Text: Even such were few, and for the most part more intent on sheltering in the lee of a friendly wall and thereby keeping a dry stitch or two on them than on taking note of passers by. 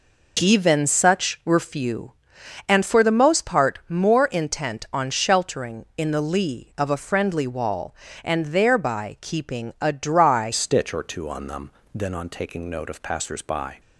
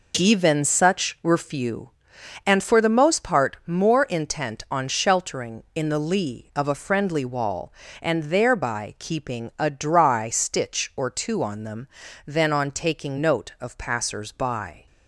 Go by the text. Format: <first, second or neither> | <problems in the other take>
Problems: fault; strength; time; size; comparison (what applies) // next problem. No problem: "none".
second | changes voice at "stitch"; from 10.5 s on; 3.2 s long